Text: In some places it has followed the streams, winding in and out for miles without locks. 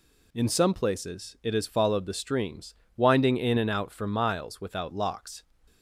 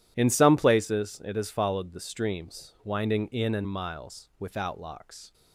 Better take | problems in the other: first | skips "out for"; at 3.6 s

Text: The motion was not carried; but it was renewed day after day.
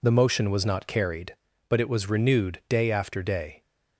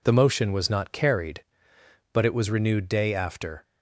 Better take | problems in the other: first | stops before "day"; at 3.6 s

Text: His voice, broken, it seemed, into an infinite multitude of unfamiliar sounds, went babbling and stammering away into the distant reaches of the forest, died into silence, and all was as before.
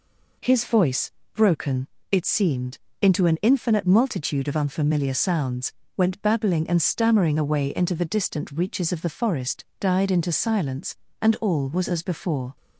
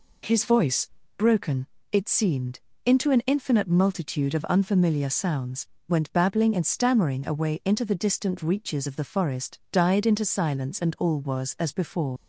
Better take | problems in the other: first | leaves "before" unfinished; at 12.1 s; 80 ms

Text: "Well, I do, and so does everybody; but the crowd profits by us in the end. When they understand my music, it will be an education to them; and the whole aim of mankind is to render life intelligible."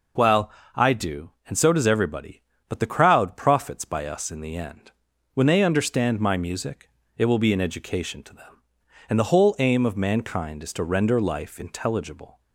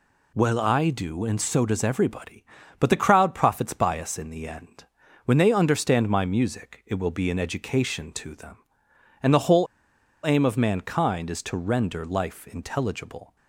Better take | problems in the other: first | pauses between "whole" and "aim"; noticeable; at 9.6 s; 0.59 s long

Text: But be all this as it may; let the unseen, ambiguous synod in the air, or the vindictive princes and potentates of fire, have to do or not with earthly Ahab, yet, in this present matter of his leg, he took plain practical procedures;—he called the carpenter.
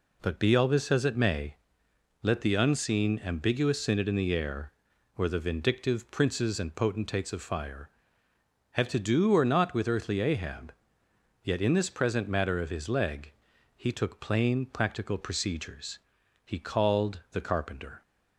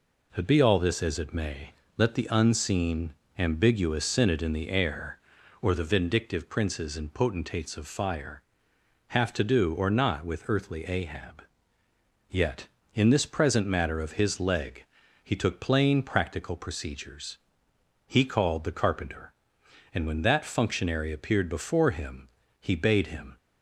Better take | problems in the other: first | goes on to say "And when that functionary appeared before him he bade him"; strong; from 19.9 s on; 3.4 s long

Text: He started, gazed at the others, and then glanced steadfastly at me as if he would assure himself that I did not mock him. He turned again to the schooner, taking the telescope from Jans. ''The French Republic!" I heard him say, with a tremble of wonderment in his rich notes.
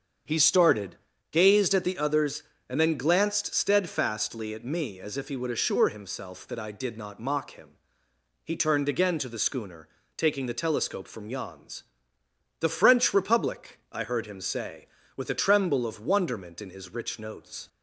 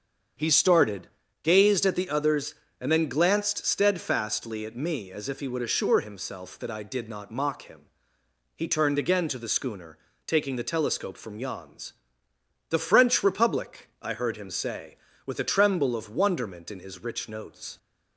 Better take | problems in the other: neither | starts louder than the rest; strong; the same in both

